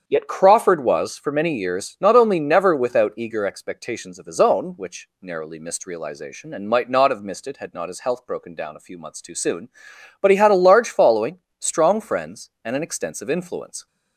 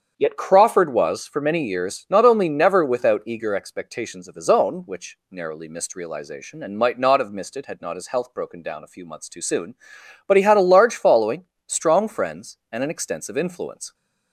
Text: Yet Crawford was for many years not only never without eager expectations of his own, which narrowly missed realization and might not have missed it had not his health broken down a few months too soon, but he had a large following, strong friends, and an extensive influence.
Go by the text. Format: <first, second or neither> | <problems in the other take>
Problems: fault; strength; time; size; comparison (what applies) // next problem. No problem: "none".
neither | starts louder than the rest; strong; the same in both